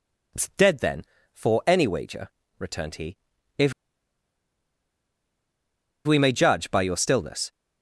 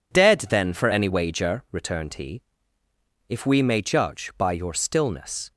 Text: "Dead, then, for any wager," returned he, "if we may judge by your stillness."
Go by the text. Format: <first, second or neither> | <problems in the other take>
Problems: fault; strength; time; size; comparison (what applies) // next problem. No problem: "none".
second | pauses between "if" and "we"; strong; at 3.7 s; 2.3 s long